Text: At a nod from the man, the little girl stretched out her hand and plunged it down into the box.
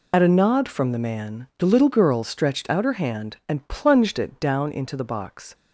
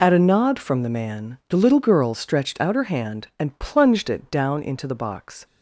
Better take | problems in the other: second | loses the start of "At"; at 0.1 s; 40 ms

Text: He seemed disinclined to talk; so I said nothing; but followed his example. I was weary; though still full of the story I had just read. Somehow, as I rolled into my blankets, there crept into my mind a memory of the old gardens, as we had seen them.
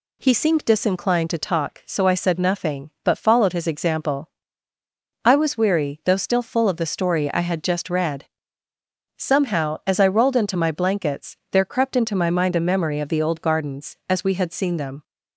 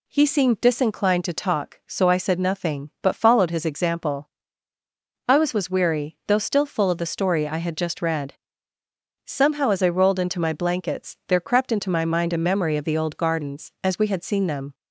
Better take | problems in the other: first | says "was" twice; at 5.5 s

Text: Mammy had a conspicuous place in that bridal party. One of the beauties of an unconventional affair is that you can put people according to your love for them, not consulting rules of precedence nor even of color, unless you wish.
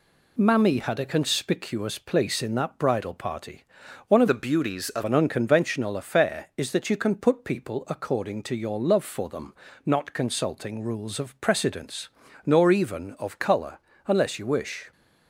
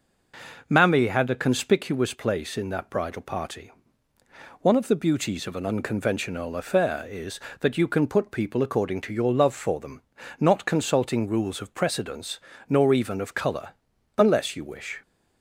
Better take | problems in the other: second | changes voice from "the" to "of"; from 4.2 to 5.0 s; 0.8 s long // pauses between "precedence" and "nor"; slight; at 12.0 s; 0.36 s long; slight in the second

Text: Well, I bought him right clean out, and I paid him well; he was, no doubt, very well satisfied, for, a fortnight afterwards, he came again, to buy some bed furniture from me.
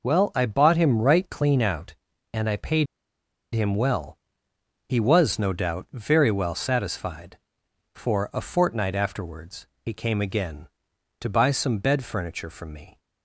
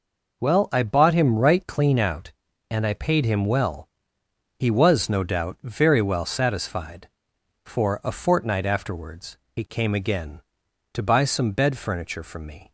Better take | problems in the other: second | pauses between "paid" and "him"; noticeable; at 2.8 s; 0.68 s long

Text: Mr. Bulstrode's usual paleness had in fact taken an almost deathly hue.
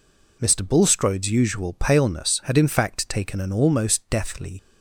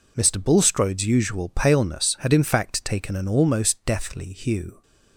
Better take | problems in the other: second | stops before "hue"; at 4.5 s

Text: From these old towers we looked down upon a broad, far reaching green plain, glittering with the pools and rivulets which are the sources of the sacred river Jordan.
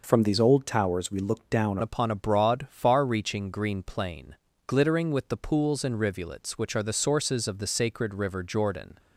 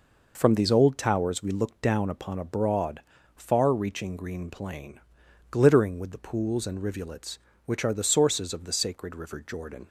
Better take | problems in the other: second | changes voice at "upon"; from 1.8 s on; 7.1 s long

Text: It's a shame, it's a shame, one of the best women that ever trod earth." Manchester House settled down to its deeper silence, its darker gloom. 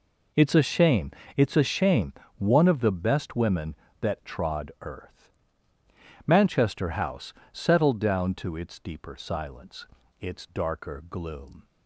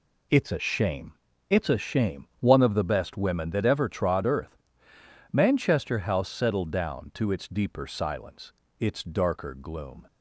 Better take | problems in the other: second | skips "ever"; at 4.1 s // pauses between "House" and "settled"; slight; at 7.3 s; 0.18 s long

